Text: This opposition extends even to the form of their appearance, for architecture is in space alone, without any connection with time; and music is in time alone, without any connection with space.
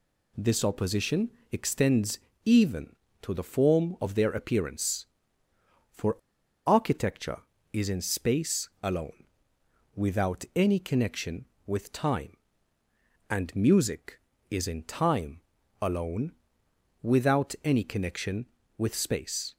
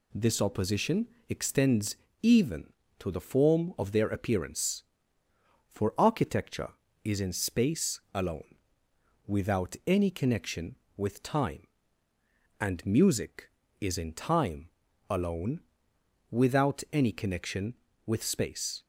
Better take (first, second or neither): second